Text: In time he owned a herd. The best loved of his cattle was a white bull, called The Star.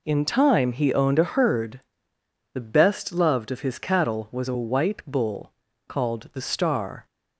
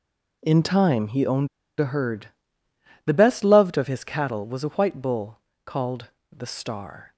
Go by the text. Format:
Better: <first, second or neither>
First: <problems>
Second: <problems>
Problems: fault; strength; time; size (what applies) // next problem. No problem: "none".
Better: first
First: none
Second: pauses between "owned" and "a"; slight; at 1.4 s; 0.31 s long // pauses between "called" and "The"; slight; at 6.0 s; 0.22 s long